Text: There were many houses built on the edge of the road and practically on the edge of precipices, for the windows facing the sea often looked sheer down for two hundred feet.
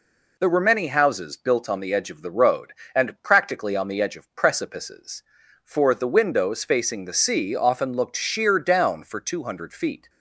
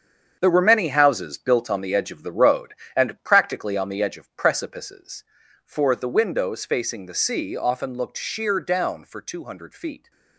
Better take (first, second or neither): first